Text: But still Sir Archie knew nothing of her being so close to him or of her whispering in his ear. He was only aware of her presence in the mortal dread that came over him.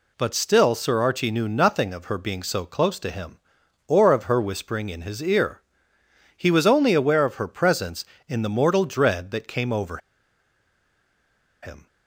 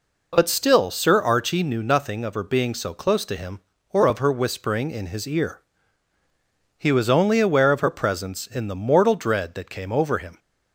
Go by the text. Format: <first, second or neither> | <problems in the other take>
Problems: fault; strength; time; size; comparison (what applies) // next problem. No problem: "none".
second | pauses between "over" and "him"; strong; at 9.9 s; 1.6 s long